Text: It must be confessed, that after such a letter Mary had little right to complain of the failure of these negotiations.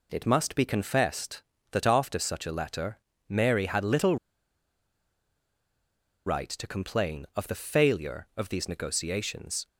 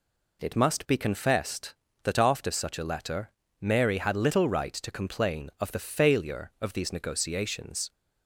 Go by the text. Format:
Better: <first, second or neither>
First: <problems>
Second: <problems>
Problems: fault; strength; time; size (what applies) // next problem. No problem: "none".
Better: second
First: pauses between "letter" and "Mary"; slight; at 2.9 s; 0.30 s long // pauses between "little" and "right"; strong; at 4.1 s; 2.0 s long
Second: pauses between "letter" and "Mary"; slight; at 3.2 s; 0.30 s long